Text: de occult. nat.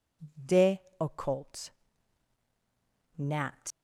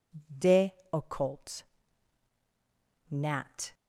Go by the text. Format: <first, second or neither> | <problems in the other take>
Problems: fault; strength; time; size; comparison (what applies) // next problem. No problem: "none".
second | pauses between "de" and "occult"; slight; at 0.8 s; 0.18 s long; slight in the second // leaves "nat" unfinished; at 3.7 s; 105 ms